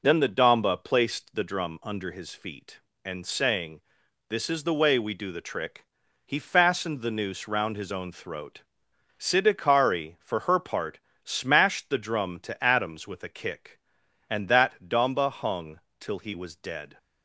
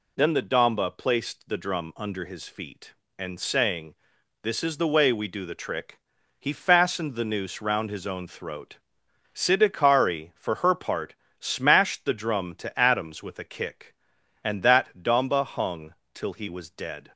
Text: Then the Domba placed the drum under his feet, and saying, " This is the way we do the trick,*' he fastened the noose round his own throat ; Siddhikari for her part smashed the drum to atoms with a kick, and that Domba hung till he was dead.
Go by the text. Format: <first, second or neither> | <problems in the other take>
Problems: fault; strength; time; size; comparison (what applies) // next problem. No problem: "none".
second | starts louder than the rest; noticeable; until 1.5 s; 5.5 dB // pauses between "part" and "smashed"; slight; at 10.9 s; 0.24 s long; slight in the second // pauses between "hung" and "till"; slight; at 15.7 s; 0.18 s long; slight in the second